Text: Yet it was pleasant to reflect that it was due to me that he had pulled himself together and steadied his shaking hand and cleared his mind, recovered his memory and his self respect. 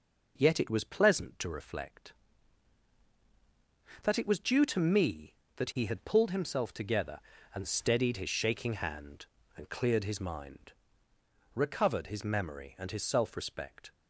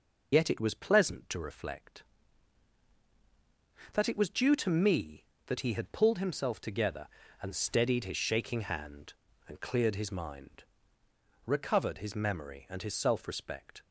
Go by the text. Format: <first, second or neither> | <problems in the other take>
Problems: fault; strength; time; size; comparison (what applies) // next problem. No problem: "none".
first | loses the start of "Yet"; at 0.3 s; 70 ms